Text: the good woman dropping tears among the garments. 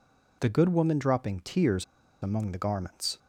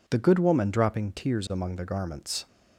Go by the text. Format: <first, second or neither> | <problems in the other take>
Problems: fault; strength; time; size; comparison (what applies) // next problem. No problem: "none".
second | pauses between "tears" and "among"; at 1.8 s; 0.37 s long